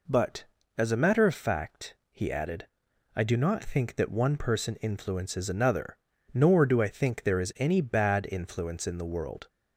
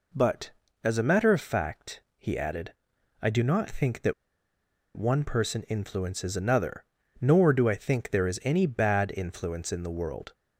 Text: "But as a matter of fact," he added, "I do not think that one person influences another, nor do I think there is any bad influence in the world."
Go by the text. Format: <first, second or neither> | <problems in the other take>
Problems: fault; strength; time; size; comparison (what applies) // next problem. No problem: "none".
first | pauses between "that" and "one"; noticeable; at 4.1 s; 0.81 s long